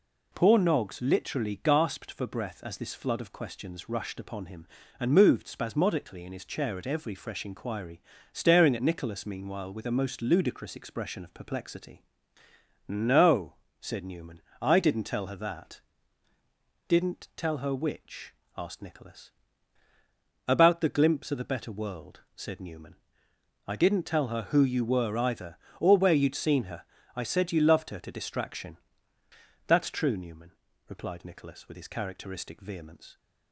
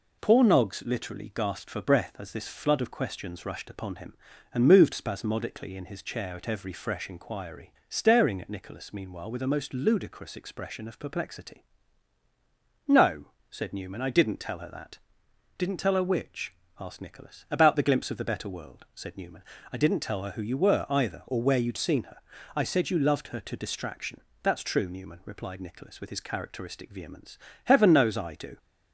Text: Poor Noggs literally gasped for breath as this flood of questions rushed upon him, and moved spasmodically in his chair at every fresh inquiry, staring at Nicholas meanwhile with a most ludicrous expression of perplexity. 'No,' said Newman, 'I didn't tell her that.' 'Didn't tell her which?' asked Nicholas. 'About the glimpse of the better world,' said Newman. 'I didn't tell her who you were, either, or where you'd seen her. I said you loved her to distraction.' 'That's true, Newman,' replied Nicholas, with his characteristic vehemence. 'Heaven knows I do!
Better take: second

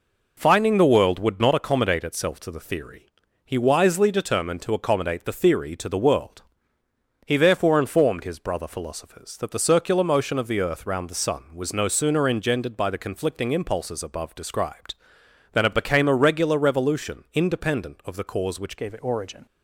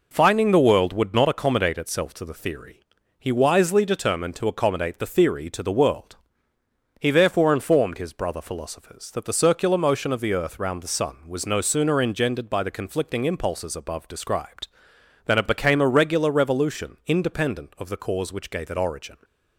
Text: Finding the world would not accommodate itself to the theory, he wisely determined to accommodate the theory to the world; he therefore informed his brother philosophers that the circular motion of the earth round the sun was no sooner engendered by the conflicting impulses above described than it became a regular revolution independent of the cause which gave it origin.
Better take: second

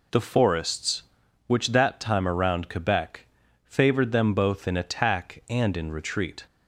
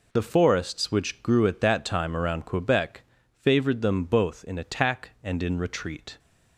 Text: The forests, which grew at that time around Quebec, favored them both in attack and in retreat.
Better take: second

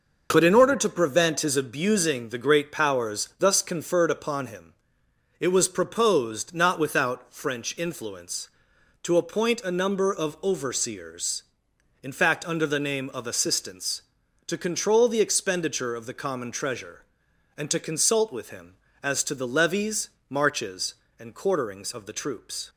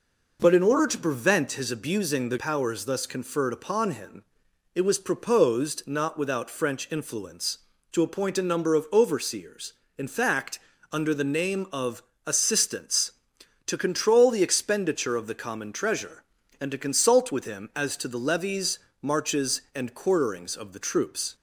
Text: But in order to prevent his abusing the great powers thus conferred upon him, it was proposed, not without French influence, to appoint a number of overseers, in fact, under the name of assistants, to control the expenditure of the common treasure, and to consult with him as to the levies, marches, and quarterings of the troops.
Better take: first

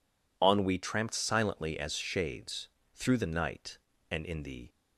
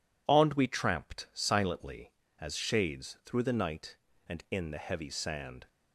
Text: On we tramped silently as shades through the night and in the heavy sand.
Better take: second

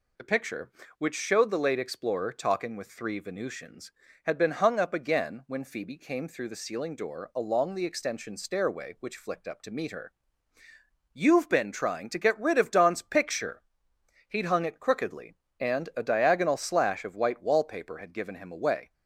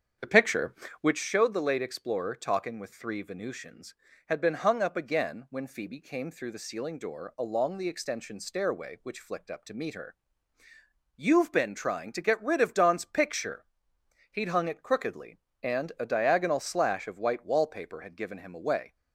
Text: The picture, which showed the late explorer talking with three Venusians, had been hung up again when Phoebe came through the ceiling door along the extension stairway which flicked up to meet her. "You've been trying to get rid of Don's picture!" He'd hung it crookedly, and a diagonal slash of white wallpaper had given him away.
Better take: first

